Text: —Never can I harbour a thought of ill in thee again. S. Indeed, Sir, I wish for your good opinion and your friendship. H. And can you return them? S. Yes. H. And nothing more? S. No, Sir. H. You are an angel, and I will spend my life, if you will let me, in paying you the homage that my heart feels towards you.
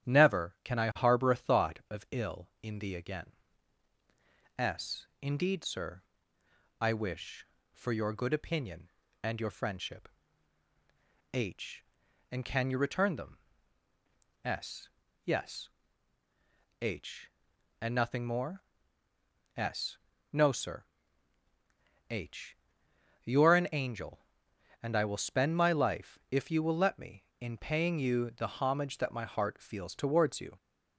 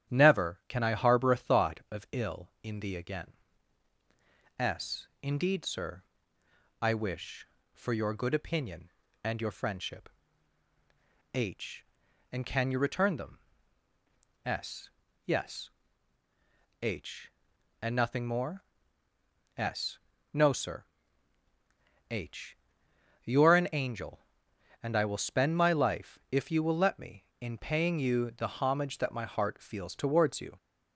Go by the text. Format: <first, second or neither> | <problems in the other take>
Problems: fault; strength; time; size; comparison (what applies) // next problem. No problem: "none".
neither | starts louder than the rest; strong; the same in both